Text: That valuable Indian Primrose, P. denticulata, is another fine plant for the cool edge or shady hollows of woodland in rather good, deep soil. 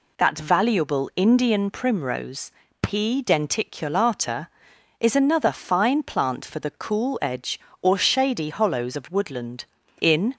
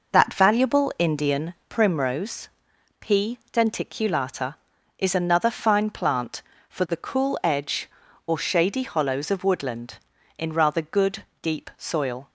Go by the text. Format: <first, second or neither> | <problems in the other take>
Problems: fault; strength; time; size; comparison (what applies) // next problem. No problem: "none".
second | stops before "rather good deep soil"; at 10.3 s